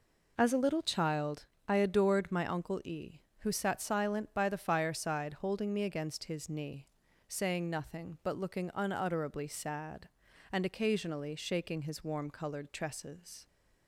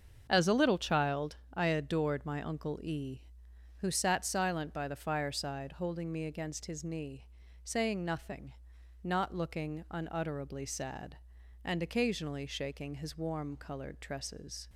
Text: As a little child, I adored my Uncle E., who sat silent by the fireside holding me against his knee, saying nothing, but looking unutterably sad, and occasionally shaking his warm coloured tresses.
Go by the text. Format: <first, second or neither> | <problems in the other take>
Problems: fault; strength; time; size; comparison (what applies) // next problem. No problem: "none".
first | starts louder than the rest; strong; until 1.3 s; 7 dB // says "not" for "but"; at 9.0 s